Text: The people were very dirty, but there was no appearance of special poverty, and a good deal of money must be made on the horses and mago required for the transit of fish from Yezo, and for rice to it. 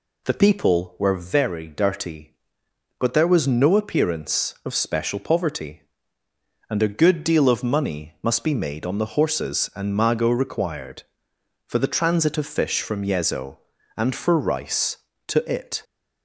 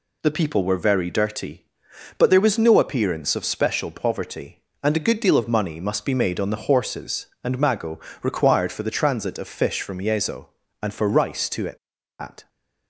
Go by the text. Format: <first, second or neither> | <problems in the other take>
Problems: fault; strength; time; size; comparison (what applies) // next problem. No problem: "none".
first | pauses between "mago" and "required"; slight; at 8.0 s; 0.22 s long // goes on to say "At"; slight; from 12.1 s on; 0.30 s long